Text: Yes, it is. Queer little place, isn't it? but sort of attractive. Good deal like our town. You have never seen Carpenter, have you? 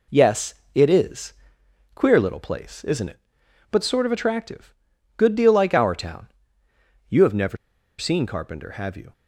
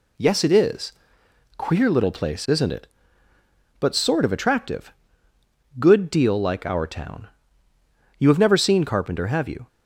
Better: second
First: pauses between "never" and "seen"; at 7.5 s; 0.43 s long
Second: none

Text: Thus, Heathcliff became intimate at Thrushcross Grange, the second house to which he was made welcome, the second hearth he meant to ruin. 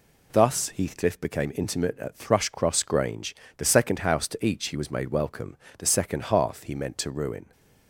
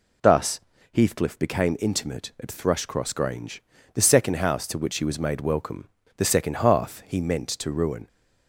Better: second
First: says "each" for "which"; at 4.4 s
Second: none

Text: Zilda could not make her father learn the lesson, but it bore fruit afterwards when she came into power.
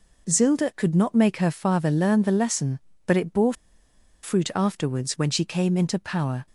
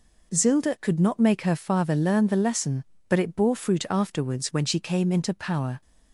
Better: second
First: pauses between "bore" and "fruit"; noticeable; at 3.5 s; 0.70 s long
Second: none

